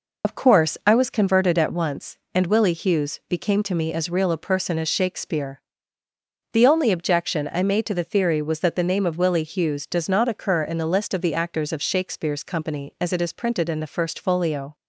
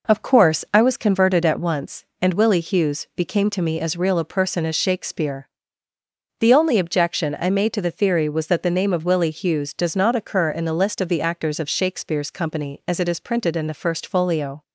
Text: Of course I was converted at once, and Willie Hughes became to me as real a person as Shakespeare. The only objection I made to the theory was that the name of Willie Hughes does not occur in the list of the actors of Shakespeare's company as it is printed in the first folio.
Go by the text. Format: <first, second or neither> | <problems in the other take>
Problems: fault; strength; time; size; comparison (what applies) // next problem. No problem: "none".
second | loses the start of "Of"; at 0.2 s; 70 ms